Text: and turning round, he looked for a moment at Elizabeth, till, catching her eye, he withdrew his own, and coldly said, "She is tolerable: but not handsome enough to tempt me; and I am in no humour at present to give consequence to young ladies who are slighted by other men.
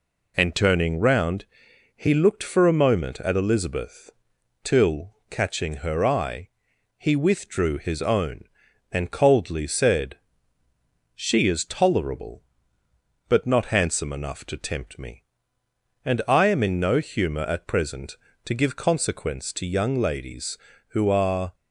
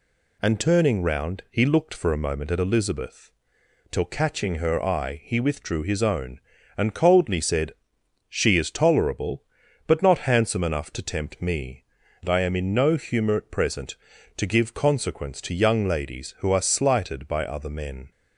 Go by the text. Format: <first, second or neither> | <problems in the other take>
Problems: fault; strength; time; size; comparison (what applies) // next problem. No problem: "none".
second | stops before "slighted by other men"; at 21.5 s